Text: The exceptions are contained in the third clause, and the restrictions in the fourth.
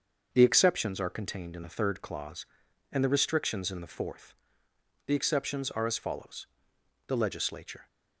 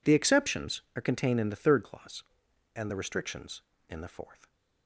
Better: second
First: starts louder than the rest; until 1.3 s; 6.5 dB // goes on to say "The exceptions are as follows The Legislature"; strong; from 5.0 s on; 2.8 s long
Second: none

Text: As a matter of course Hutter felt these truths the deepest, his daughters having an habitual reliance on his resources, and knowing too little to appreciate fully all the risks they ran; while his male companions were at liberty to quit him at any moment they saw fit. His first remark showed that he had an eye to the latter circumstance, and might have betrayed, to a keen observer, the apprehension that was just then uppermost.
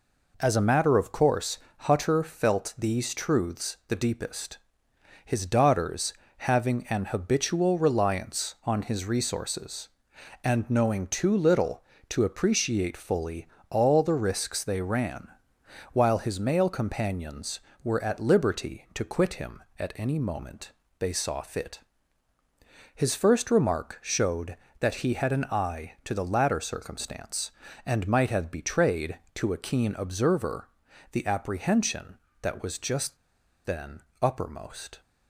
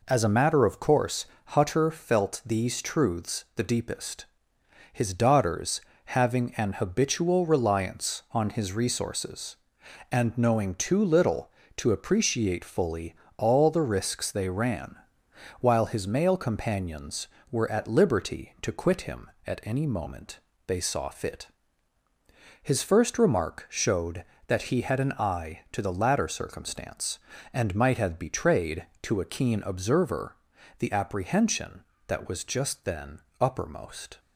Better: second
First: pauses between "course" and "Hutter"; slight; at 1.5 s; 0.20 s long // pauses between "daughters" and "having"; slight; at 6.1 s; 0.28 s long // pauses between "fully" and "all"; slight; at 13.4 s; 0.22 s long // pauses between "moment" and "they"; slight; at 20.7 s; 0.28 s long // pauses between "just" and "then"; noticeable; at 33.1 s; 0.49 s long // pauses between "then" and "uppermost"; slight; at 34.0 s; 0.20 s long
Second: pauses between "course" and "Hutter"; slight; at 1.2 s; 0.20 s long // pauses between "daughters" and "having"; slight; at 5.7 s; 0.28 s long // pauses between "fully" and "all"; slight; at 13.1 s; 0.22 s long // pauses between "moment" and "they"; slight; at 20.3 s; 0.28 s long // pauses between "then" and "uppermost"; slight; at 33.1 s; 0.20 s long

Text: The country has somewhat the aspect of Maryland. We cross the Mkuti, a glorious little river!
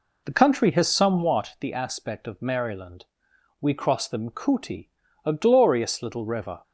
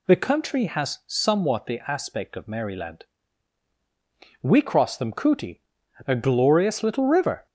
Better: second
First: starts louder than the rest; until 1.4 s; 3.5 dB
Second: none

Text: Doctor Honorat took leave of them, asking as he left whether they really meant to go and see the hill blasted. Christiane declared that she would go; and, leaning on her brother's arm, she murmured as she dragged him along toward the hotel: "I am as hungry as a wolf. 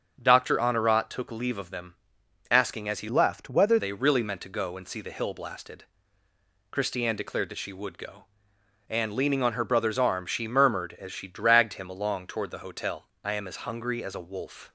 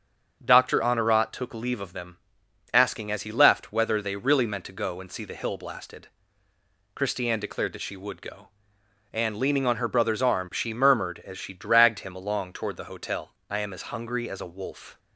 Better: second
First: starts louder than the rest; strong; until 1.2 s; 7 dB // changes voice from "left" to "whether"; from 3.0 to 3.7 s; 0.7 s long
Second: starts louder than the rest; strong; until 1.4 s; 7 dB

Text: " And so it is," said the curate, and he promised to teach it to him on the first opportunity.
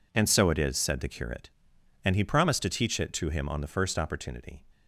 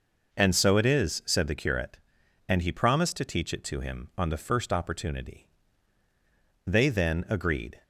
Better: first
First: none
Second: goes on to say "They then agreed"; noticeable; from 6.6 s on; 1.1 s long

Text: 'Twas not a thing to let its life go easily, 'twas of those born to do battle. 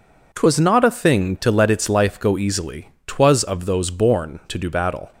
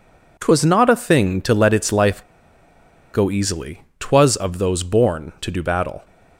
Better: first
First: none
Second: pauses between "life" and "go"; noticeable; at 2.2 s; 0.92 s long

